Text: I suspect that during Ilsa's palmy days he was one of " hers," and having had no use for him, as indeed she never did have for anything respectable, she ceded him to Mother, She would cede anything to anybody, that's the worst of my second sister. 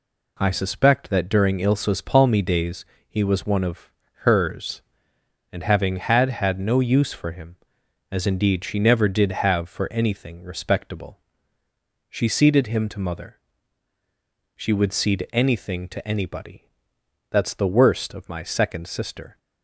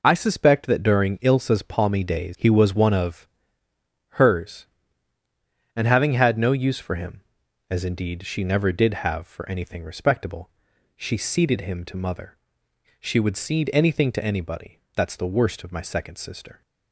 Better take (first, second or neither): second